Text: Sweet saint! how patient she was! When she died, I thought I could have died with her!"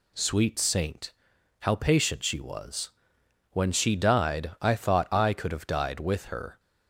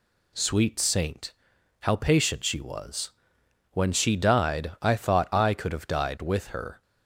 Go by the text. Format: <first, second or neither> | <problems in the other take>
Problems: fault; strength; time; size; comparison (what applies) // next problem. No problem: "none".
neither | none